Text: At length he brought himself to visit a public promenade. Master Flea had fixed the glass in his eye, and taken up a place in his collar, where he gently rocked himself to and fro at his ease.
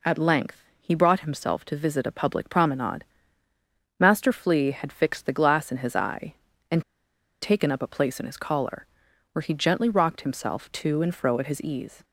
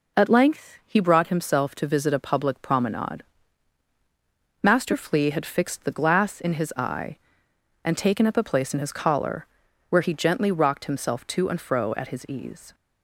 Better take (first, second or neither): second